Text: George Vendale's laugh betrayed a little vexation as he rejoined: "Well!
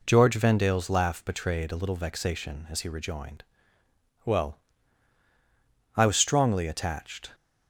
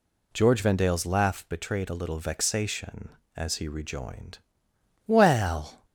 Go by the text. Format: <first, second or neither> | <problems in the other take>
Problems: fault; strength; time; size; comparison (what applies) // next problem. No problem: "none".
second | goes on to say "I was strongly attached"; from 5.9 s on; 1.3 s long